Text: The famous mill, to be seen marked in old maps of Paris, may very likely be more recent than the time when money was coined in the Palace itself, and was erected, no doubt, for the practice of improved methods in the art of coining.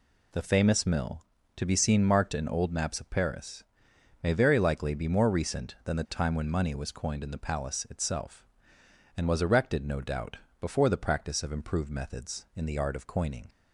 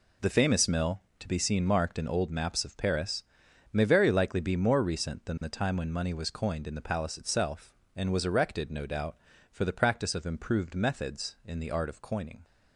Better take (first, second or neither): second